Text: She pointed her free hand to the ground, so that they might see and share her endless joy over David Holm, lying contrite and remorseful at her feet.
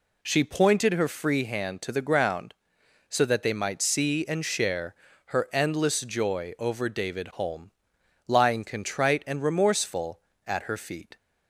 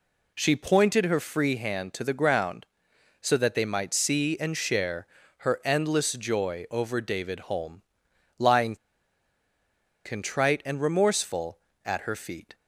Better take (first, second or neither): first